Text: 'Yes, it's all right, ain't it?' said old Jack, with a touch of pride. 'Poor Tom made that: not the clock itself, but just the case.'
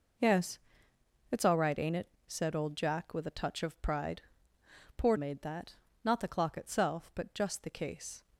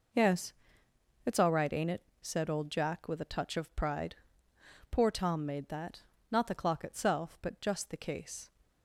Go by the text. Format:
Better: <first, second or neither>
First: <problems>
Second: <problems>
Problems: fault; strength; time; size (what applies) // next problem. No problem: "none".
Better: second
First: skips "Tom"; at 5.1 s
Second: none